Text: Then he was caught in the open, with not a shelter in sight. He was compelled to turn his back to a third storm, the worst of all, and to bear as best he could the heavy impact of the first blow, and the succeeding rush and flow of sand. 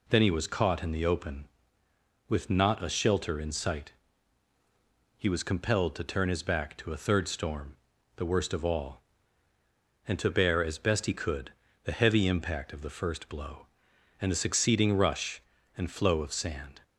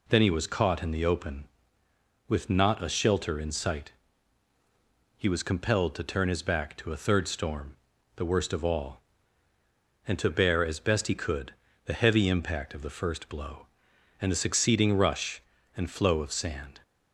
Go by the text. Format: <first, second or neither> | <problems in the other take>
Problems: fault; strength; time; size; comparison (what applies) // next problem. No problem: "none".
neither | pauses between "could" and "the"; slight; the same in both